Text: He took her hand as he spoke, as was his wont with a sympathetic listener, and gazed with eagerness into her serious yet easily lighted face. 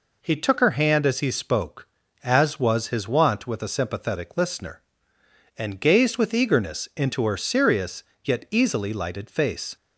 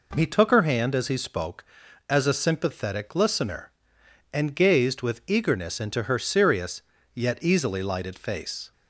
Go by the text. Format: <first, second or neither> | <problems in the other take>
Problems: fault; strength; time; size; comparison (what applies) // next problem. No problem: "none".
first | skips "was his wont with"; at 2.2 s // pauses between "serious" and "yet"; slight; at 6.8 s; 0.32 s long; slight in the first